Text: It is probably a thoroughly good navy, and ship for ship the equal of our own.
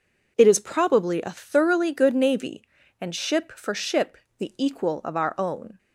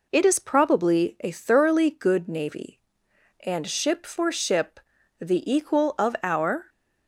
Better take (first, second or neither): first